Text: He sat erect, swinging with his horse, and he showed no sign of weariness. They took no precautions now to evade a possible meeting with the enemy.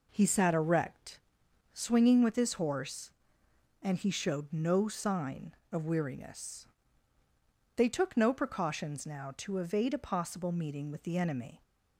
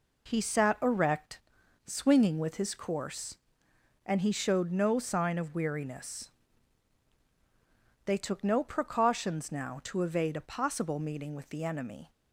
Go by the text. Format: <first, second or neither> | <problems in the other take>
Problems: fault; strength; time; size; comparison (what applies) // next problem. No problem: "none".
first | says "course" for "horse"; at 2.7 s